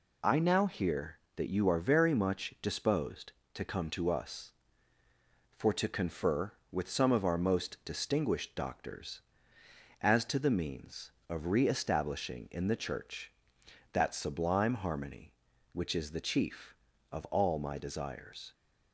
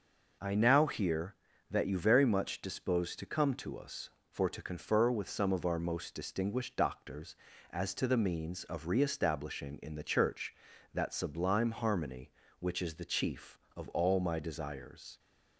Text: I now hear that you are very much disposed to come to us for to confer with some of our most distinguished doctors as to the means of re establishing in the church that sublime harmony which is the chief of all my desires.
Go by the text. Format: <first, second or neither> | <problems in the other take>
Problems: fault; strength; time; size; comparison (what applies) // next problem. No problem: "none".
first | skips "are"; at 1.9 s